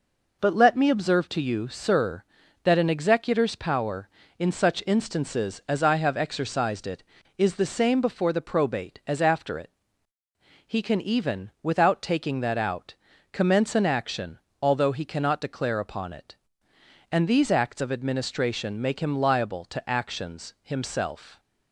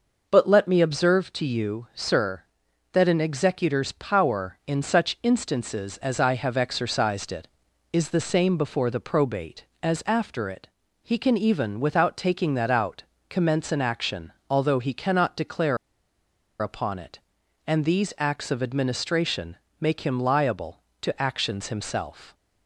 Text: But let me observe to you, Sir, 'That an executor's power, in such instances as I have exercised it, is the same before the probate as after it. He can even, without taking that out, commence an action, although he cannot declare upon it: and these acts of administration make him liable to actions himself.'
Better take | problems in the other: first | pauses between "declare" and "upon"; noticeable; at 15.7 s; 0.84 s long // pauses between "administration" and "make"; slight; at 19.5 s; 0.24 s long

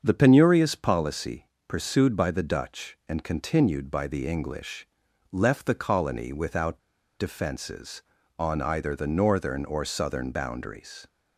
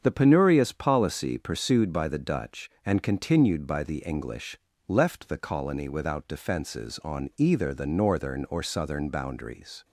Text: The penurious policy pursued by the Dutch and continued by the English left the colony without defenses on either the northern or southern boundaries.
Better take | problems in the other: second | starts louder than the rest; until 1.0 s; 7 dB; strong in the second // pauses between "policy" and "pursued"; slight; at 1.4 s; 0.18 s long // pauses between "English" and "left"; noticeable; at 4.8 s; 0.46 s long; slight in the second // pauses between "without" and "defenses"; at 6.7 s; 0.40 s long

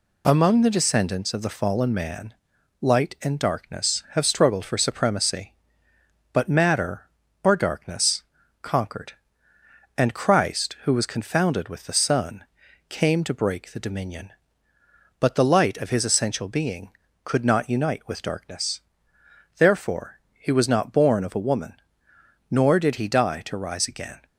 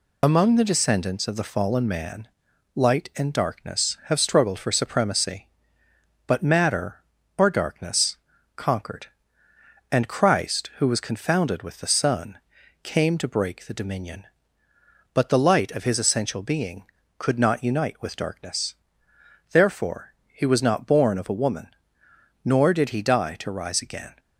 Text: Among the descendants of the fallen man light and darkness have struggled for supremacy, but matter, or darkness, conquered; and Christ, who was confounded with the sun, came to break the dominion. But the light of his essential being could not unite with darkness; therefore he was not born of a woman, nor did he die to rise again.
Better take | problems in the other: first | loses the start of "Among"; at 0.2 s; 40 ms // pauses between "man" and "light"; noticeable; at 2.2 s; 0.48 s long; noticeable in the first

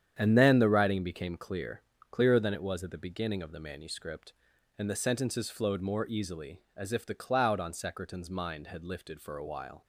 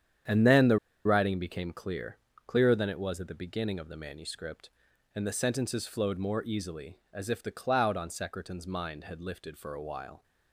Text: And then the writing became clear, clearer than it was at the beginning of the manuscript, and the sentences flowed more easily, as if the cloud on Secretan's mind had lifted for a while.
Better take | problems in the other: first | starts louder than the rest; strong; until 1.5 s; 9 dB; strong in the first // pauses between "the" and "writing"; slight; at 0.7 s; 0.26 s long

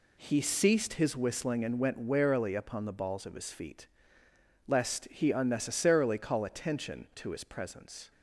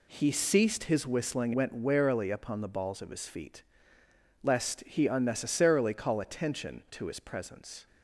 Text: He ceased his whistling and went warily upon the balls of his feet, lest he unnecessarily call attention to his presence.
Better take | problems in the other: first | skips "and"; at 1.5 s

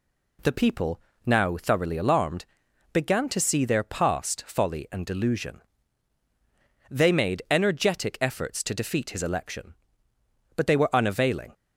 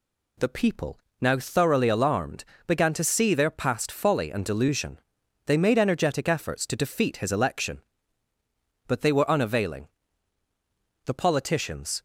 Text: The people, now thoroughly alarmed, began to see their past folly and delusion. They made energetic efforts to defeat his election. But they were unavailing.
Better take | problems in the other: first | goes on to say "The politicians"; noticeable; from 11.0 s on; 0.98 s long

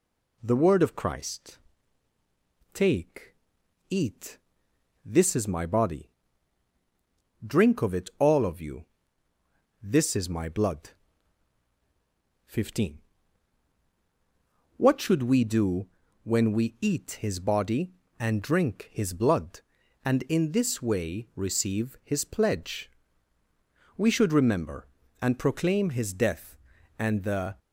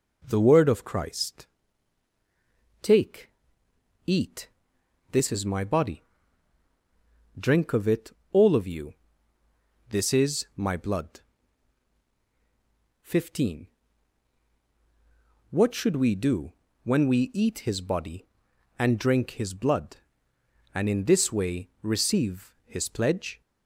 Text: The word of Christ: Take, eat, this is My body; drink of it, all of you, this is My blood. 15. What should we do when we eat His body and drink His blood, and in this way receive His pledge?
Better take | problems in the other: second | pauses between "do" and "when"; slight; at 15.8 s; 0.36 s long; slight in the second // goes on to say "We should remember and proclaim His death and the"; strong; from 23.9 s on; 3.6 s long

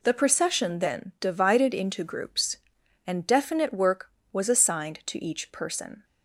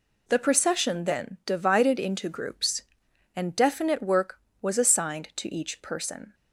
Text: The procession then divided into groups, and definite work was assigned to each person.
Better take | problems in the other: neither | none

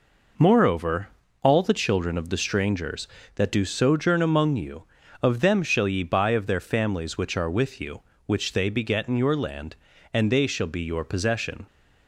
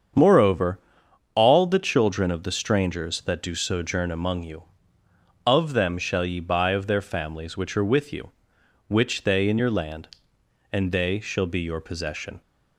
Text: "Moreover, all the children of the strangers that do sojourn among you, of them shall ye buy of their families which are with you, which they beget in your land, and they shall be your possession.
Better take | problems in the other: first | starts louder than the rest; strong; until 1.7 s; 7.5 dB // skips "beget"; at 9.4 s

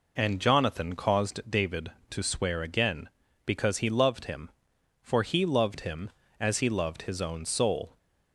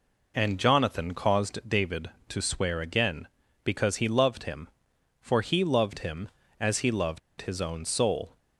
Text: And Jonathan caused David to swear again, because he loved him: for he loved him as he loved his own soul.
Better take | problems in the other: first | pauses between "loved" and "his"; slight; at 7.1 s; 0.20 s long

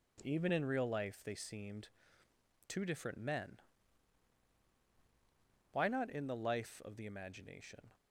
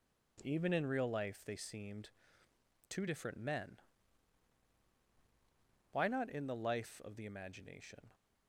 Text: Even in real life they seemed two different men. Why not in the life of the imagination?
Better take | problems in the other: neither | pauses between "seemed" and "two"; noticeable; the same in both

